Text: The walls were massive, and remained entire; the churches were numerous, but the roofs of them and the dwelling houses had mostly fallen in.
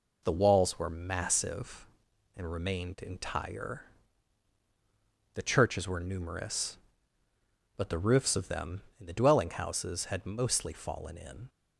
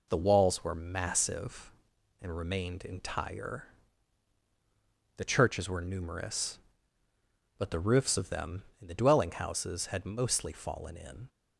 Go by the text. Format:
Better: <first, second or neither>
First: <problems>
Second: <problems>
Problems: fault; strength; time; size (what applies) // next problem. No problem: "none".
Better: neither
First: none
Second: none